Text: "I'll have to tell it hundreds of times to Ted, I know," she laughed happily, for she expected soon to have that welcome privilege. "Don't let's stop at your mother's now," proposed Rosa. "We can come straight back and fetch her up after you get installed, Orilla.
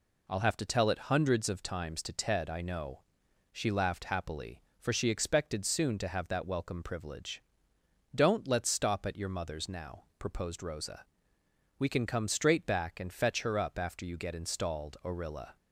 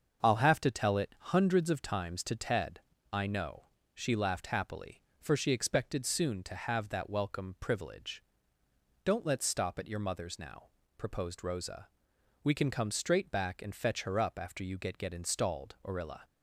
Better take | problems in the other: first | starts louder than the rest; until 1.2 s; 6.5 dB // says "get" twice; at 14.9 s

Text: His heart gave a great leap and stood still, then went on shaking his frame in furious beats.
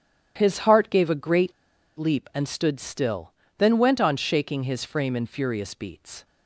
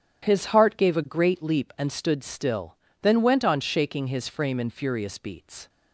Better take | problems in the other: second | starts louder than the rest; strong; until 1.3 s; 9.5 dB; strong in the second // pauses between "great" and "leap"; noticeable; at 1.5 s; 0.46 s long

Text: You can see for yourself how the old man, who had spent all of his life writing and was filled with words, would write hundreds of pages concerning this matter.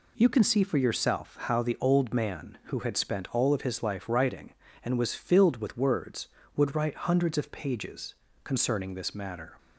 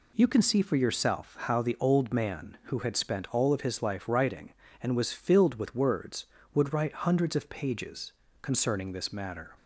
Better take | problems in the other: neither | pauses between "pages" and "concerning"; slight; the same in both

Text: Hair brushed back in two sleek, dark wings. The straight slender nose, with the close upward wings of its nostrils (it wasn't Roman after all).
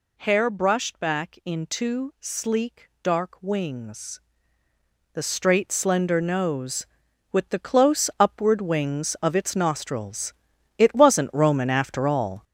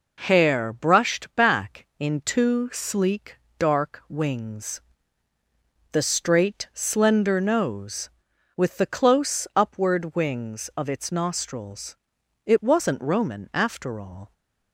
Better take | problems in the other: second | gets louder; strong; throughout; 7.5 dB

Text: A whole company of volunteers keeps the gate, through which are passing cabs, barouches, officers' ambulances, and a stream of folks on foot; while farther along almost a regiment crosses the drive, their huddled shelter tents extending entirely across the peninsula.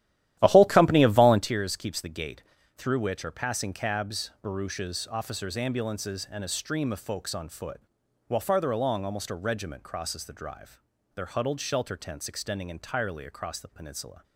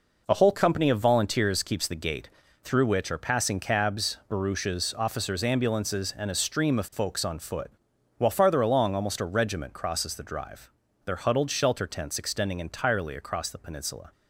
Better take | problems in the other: second | starts louder than the rest; strong; until 1.5 s; 13 dB

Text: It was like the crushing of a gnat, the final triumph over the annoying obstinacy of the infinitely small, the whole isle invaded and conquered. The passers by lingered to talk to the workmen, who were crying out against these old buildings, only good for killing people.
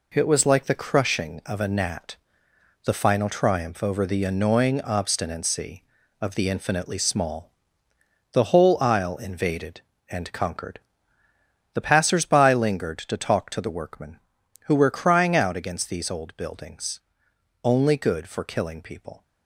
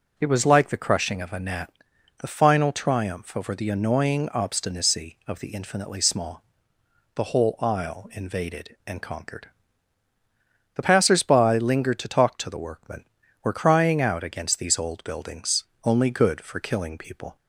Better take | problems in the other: first | skips "who"; at 13.2 s

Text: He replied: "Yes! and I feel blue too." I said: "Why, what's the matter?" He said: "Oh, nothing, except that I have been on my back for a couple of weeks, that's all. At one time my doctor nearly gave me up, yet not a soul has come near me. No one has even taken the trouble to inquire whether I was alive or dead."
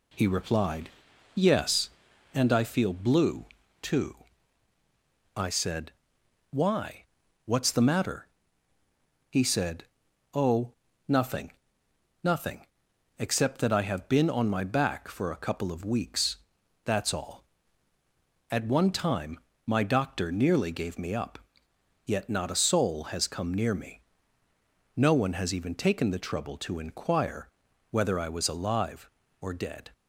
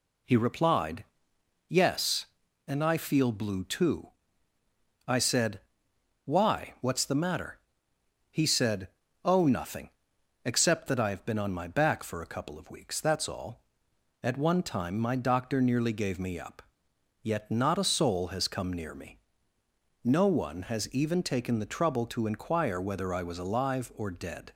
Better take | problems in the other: second | pauses between "blue" and "too"; slight; at 3.4 s; 0.34 s long // says "nothing" twice; at 12.2 s // pauses between "time" and "my"; slight; at 19.4 s; 0.26 s long // pauses between "inquire" and "whether"; at 27.4 s; 0.42 s long

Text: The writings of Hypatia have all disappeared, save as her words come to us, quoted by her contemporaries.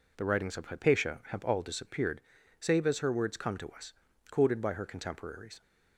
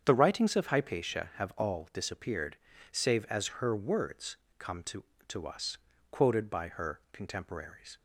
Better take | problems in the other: first | starts louder than the rest; strong; until 1.0 s; 7.5 dB // pauses between "words" and "come"; slight; at 4.3 s; 0.22 s long // says "to" twice; at 5.2 s

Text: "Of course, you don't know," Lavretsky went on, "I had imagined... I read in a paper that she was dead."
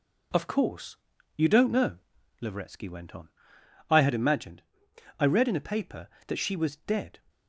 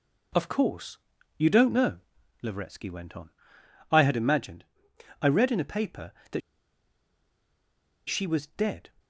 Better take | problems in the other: first | pauses between "that" and "she"; strong; at 6.4 s; 1.6 s long

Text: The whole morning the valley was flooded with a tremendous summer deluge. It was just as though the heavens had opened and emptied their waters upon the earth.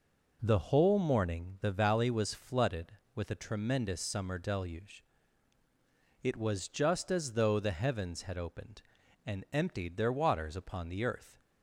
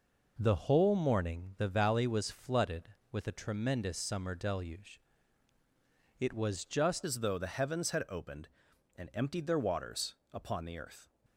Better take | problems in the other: first | changes voice at "as"; from 7.0 s on; 4.0 s long // pauses between "waters" and "upon"; slight; at 10.1 s; 0.18 s long

